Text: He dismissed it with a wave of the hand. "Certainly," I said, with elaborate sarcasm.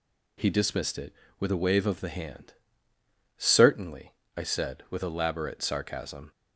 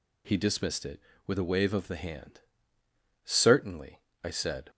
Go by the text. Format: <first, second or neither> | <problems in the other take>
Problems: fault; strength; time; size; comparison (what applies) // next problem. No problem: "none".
first | stops before "with elaborate sarcasm"; at 4.6 s